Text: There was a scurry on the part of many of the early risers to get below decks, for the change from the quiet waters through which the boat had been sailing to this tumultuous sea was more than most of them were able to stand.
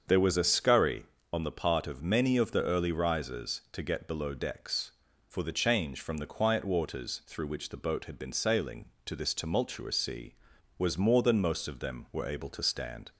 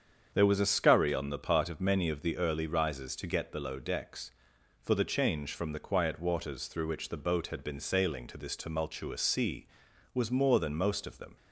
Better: first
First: starts louder than the rest; until 1.3 s; 7 dB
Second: starts louder than the rest; strong; until 1.3 s; 7.5 dB // stops before "were able to stand"; at 11.3 s

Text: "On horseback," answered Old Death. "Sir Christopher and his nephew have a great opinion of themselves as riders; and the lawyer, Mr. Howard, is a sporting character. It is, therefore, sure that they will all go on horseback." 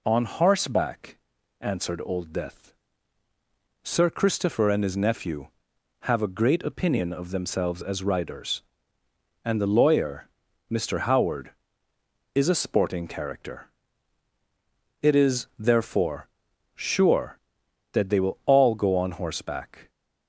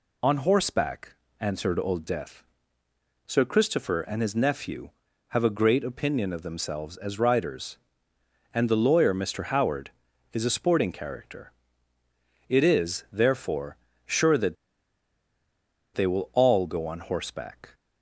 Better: first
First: none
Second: pauses between "that" and "they"; strong; at 14.5 s; 1.4 s long

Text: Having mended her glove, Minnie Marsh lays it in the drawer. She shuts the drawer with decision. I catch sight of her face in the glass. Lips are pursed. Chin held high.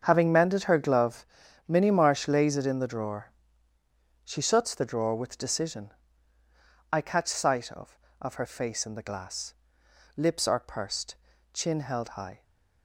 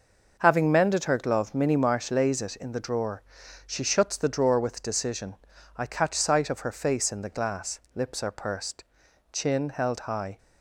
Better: second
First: starts louder than the rest; until 1.0 s; 7 dB // says "of" twice; at 8.2 s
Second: none

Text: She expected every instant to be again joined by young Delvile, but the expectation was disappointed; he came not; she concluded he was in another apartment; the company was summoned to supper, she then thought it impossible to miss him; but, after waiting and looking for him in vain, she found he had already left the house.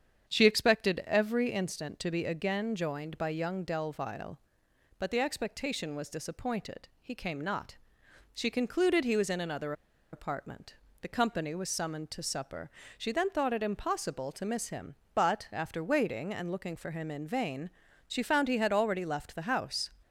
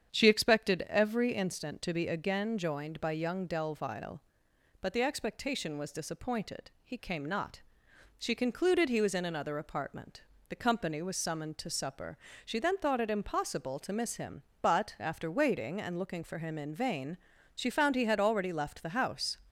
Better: second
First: starts louder than the rest; strong; until 1.3 s; 8 dB // pauses between "another" and "apartment"; at 9.7 s; 0.39 s long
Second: starts louder than the rest; strong; until 1.1 s; 8 dB

